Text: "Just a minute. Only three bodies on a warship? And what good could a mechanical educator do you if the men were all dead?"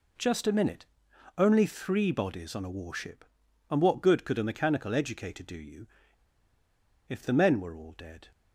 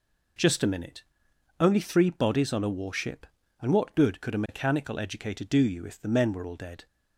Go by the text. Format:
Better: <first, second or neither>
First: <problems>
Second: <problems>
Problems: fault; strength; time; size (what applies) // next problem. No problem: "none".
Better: second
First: pauses between "you" and "if"; at 5.8 s; 1.2 s long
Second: none